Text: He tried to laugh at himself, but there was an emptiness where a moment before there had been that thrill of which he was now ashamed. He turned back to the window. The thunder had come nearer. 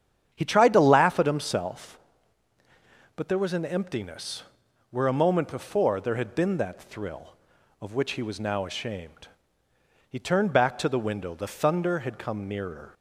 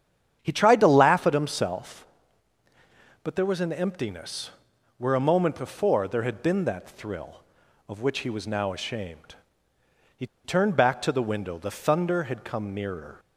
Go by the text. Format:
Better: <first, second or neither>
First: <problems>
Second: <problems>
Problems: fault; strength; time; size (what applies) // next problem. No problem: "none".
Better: first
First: starts louder than the rest; strong; until 1.3 s; 8.5 dB // pauses between "emptiness" and "where"; noticeable; at 4.4 s; 0.46 s long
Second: starts louder than the rest; strong; until 1.4 s; 8.5 dB // pauses between "emptiness" and "where"; noticeable; at 4.5 s; 0.46 s long // pauses between "He" and "turned"; slight; at 10.2 s; 0.18 s long